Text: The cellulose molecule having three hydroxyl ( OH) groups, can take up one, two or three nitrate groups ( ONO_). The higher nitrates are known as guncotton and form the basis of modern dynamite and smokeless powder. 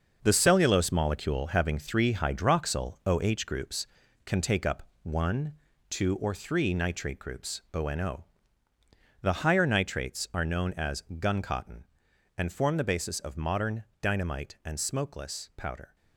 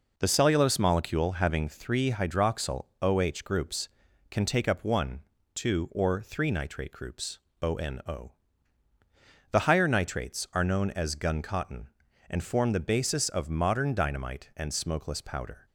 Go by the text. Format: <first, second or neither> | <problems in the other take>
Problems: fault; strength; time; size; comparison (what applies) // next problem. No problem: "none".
second | gets quieter; strong; throughout; 8.5 dB // pauses between "up" and "one"; slight; at 4.8 s; 0.18 s long // pauses between "modern" and "dynamite"; slight; at 13.8 s; 0.18 s long